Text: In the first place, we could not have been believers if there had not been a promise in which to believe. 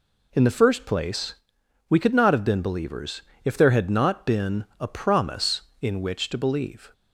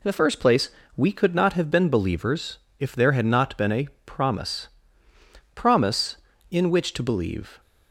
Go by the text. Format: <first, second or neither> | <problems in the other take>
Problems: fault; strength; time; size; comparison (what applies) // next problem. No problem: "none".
first | pauses between "believers" and "if"; slight; at 2.5 s; 0.22 s long; slight in the first // pauses between "a" and "promise"; slight; at 3.8 s; 0.18 s long // says "promise" twice; at 5.5 s